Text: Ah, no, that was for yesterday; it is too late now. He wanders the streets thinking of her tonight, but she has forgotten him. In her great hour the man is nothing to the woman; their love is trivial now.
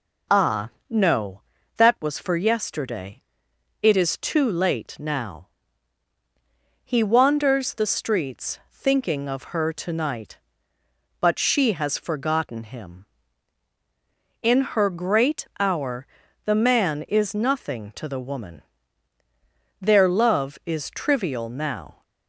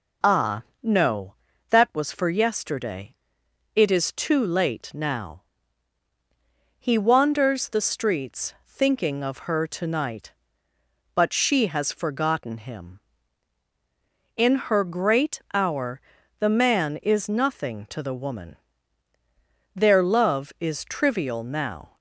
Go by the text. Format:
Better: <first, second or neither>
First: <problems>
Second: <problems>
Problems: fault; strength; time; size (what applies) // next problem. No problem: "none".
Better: neither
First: pauses between "hour" and "the"; at 16.0 s; 0.38 s long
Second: pauses between "hour" and "the"; at 16.0 s; 0.38 s long